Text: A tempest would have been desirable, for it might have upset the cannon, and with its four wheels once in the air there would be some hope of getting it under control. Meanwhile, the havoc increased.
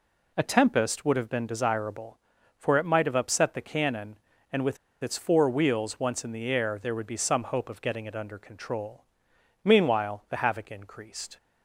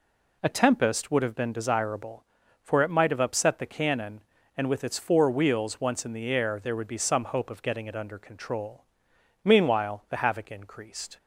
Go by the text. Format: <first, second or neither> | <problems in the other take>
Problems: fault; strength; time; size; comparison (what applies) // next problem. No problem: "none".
second | pauses between "with" and "its"; slight; at 4.7 s; 0.25 s long